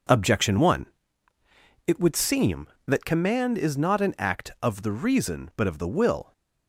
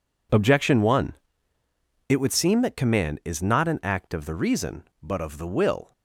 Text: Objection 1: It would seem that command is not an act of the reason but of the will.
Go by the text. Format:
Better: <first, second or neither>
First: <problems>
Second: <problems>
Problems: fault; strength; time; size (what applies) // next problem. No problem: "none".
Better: neither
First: none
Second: none